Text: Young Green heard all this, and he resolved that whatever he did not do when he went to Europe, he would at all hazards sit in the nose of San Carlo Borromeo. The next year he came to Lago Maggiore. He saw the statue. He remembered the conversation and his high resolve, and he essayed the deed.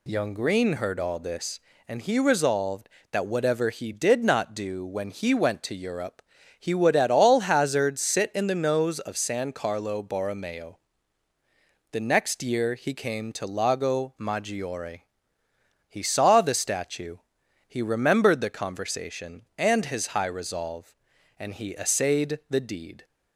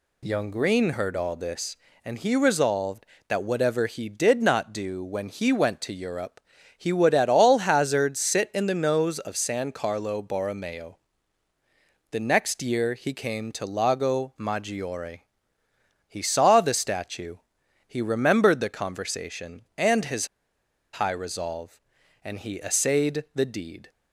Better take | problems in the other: first | pauses between "his" and "high"; noticeable; at 20.2 s; 0.65 s long

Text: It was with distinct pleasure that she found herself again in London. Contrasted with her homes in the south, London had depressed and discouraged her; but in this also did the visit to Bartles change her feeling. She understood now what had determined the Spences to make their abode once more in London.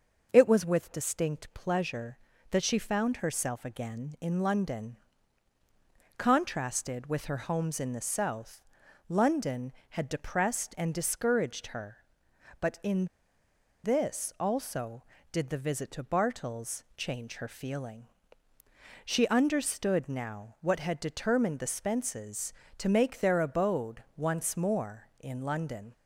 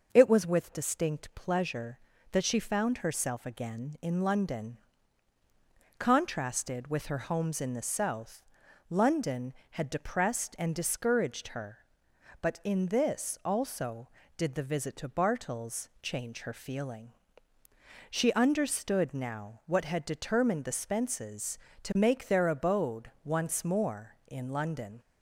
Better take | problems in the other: second | pauses between "in" and "this"; noticeable; at 13.0 s; 0.78 s long // pauses between "Bartles" and "change"; slight; at 16.8 s; 0.16 s long; slight in the second

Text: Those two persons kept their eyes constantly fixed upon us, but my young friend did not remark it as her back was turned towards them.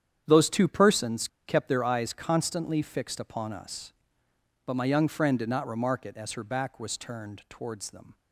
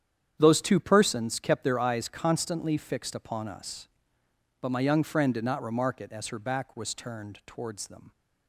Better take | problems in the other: second | starts louder than the rest; strong; until 1.2 s; 9 dB; strong in the second // pauses between "persons" and "kept"; slight; at 1.2 s; 0.18 s long

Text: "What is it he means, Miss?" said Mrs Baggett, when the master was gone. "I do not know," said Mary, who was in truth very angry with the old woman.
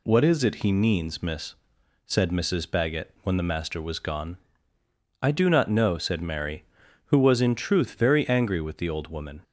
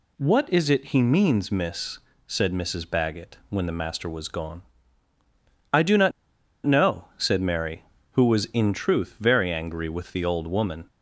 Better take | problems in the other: first | pauses between "not" and "know"; noticeable; at 6.1 s; 0.54 s long

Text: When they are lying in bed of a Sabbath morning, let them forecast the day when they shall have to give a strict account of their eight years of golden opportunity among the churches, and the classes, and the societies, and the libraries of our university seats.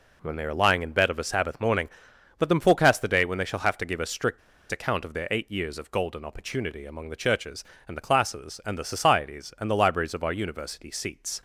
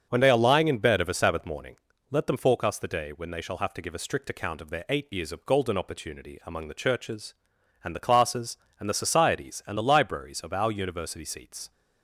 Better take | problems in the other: second | pauses between "strict" and "account"; slight; at 4.3 s; 0.31 s long

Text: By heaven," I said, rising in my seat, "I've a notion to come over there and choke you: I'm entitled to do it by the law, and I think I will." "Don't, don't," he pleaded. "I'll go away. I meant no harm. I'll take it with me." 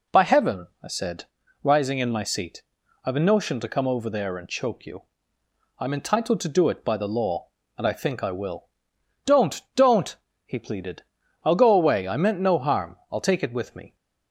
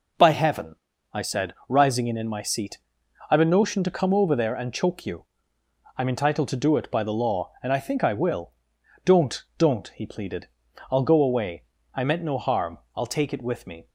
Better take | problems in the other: first | says "in" twice; at 2.1 s

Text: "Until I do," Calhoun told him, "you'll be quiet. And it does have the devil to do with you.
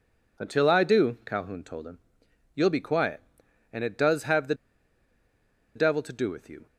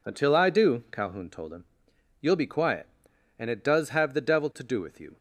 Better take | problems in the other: second | pauses between "the" and "devil"; at 4.5 s; 1.2 s long

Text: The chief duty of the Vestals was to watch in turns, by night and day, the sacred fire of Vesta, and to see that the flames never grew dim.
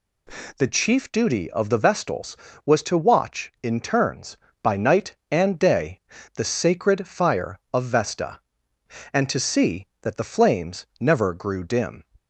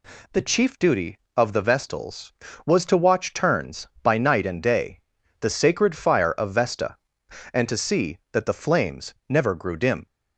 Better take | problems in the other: first | skips "in"; at 3.3 s

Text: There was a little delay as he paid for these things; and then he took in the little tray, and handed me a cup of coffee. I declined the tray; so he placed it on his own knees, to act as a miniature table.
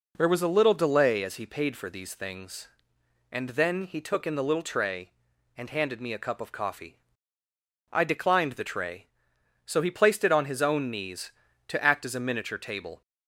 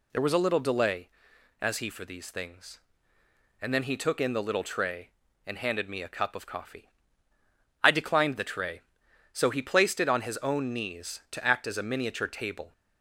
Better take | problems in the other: first | skips "paid"; at 1.9 s

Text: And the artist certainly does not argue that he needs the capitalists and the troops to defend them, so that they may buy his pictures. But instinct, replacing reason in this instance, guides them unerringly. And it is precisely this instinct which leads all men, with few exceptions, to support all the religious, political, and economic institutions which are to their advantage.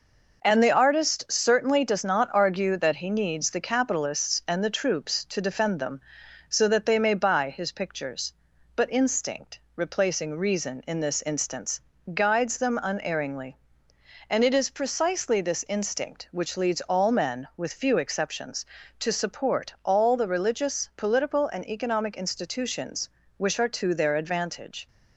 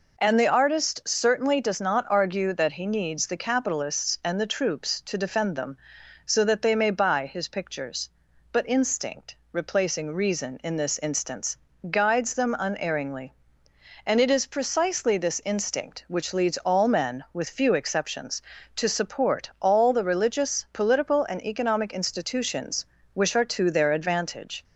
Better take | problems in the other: second | gets quieter; noticeable; throughout; 4.5 dB

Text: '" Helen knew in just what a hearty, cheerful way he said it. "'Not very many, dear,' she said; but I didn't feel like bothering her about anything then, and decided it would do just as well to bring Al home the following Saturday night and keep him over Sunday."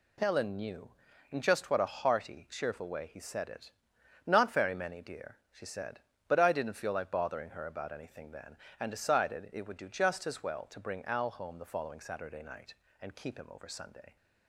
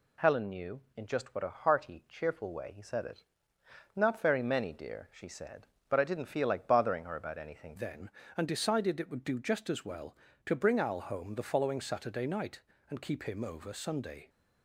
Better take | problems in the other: first | changes voice at "then"; from 7.7 s on; 6.5 s long

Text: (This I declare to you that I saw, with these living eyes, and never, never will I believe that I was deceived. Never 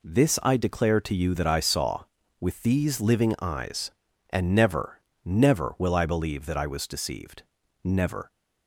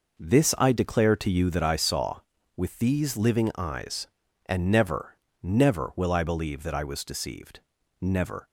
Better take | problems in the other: first | starts louder than the rest; noticeable; until 1.7 s; 5 dB

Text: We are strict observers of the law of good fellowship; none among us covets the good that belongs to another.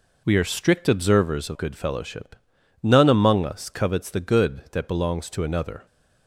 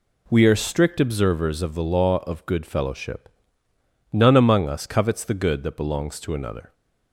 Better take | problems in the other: second | skips "the law of"; at 1.5 s

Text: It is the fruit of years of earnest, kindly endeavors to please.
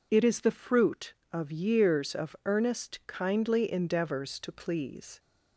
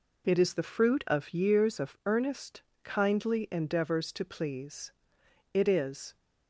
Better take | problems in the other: first | goes on to say "It is"; noticeable; from 5.5 s on; 0.62 s long

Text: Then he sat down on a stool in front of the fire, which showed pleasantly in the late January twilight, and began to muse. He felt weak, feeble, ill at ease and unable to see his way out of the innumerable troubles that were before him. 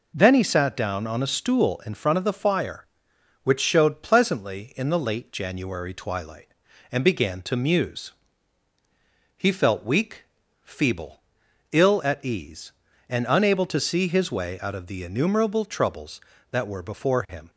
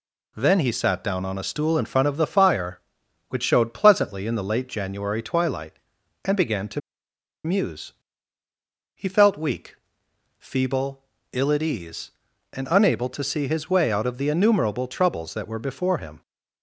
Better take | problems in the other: first | pauses between "to" and "muse"; noticeable; at 6.8 s; 0.65 s long

